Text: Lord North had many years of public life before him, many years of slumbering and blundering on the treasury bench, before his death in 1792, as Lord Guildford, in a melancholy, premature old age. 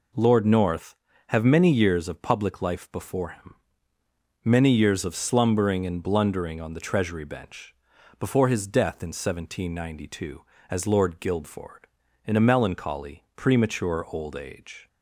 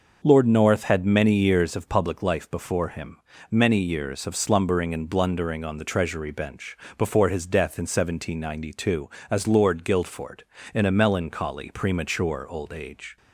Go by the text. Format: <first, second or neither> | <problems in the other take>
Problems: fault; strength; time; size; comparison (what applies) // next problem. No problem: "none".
second | says "have" for "had"; at 1.2 s